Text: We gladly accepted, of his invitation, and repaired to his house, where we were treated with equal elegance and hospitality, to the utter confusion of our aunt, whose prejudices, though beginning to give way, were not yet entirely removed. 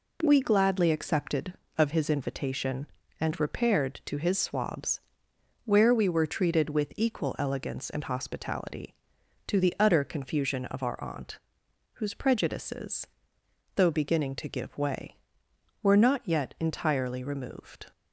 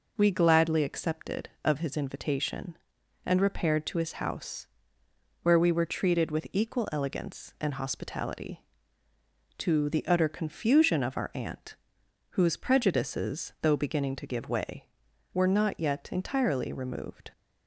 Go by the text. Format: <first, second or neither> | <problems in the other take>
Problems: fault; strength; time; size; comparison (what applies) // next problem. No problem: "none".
second | says "swabs" for "house"; at 4.3 s